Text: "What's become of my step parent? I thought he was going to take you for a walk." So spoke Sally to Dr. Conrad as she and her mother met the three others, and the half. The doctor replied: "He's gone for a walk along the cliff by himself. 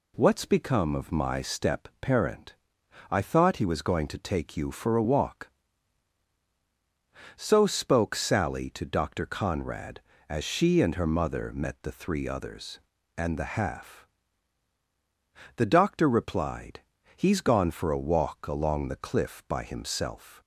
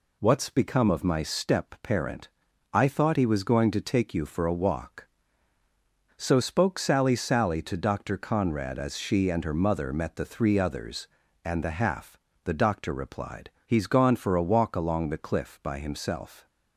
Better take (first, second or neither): first